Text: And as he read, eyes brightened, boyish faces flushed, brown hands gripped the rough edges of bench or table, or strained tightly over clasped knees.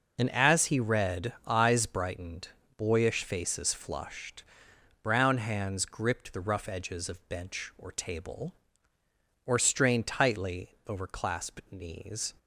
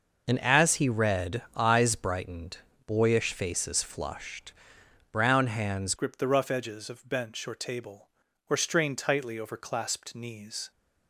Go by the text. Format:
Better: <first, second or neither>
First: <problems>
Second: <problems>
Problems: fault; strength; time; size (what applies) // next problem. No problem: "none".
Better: first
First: none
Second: changes voice at "gripped"; from 5.9 s on; 4.8 s long